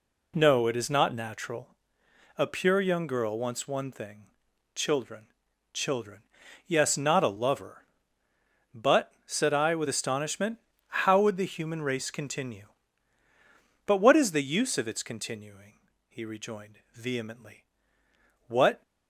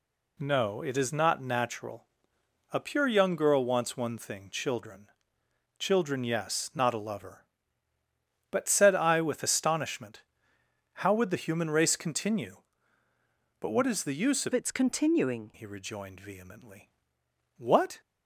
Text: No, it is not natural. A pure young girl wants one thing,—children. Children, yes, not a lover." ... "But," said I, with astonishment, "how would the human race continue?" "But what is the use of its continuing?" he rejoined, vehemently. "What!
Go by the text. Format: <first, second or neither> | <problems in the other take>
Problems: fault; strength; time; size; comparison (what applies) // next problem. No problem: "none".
first | changes voice from "its" to "continuing"; from 14.5 to 15.5 s; 1.0 s long